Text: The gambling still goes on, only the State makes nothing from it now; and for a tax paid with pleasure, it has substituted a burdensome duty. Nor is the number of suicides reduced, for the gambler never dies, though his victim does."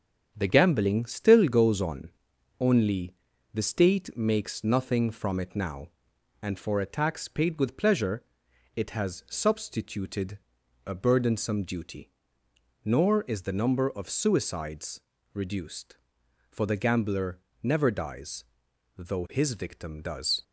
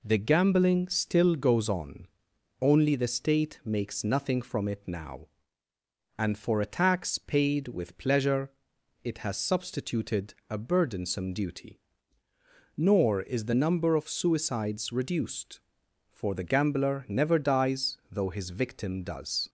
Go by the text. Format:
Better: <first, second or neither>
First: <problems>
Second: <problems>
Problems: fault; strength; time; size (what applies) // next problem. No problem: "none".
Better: second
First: gets quieter; noticeable; throughout; 4.5 dB // pauses between "only" and "the"; at 3.1 s; 0.40 s long // pauses between "substituted" and "a"; noticeable; at 10.3 s; 0.48 s long // pauses between "suicides" and "reduced"; slight; at 15.0 s; 0.34 s long // pauses between "gambler" and "never"; slight; at 17.3 s; 0.24 s long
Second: none